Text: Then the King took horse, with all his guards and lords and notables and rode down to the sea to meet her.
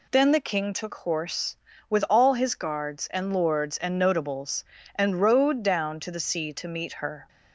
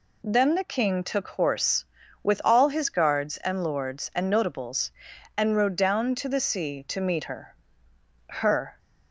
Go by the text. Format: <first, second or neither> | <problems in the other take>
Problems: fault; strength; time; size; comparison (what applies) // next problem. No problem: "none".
first | says "her" twice; at 8.2 s